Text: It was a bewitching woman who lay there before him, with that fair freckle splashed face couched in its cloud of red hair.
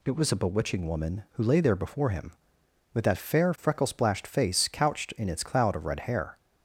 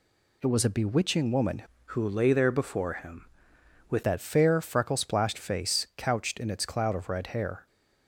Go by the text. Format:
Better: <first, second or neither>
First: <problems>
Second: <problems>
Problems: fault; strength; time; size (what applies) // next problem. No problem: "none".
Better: first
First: none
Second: changes voice from "who" to "with"; from 1.8 to 4.0 s; 2.2 s long